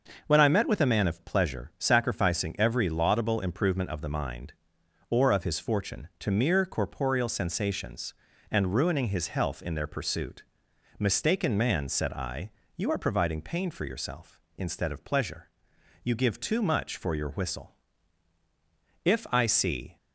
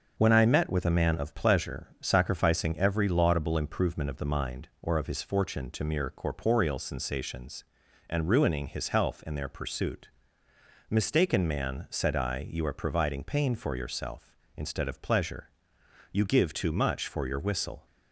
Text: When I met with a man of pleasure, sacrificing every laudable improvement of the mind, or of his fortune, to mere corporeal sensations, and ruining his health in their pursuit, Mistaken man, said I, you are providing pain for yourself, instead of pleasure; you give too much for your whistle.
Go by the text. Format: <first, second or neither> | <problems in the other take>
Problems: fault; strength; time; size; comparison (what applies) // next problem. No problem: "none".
second | starts louder than the rest; noticeable; until 1.2 s; 6 dB; also in the second // goes on to say "If I see"; noticeable; from 19.0 s on; 0.92 s long